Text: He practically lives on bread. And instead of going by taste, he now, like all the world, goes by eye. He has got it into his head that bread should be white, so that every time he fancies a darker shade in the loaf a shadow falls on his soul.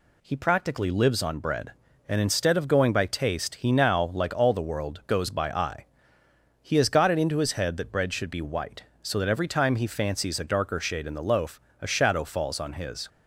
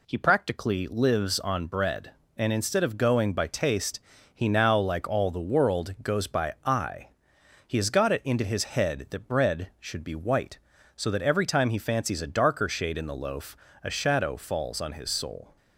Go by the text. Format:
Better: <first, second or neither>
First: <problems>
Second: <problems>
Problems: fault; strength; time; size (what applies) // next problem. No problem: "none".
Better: second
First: pauses between "loaf" and "a"; slight; at 11.5 s; 0.22 s long // stops before "soul"; at 13.0 s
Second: pauses between "loaf" and "a"; slight; at 13.5 s; 0.26 s long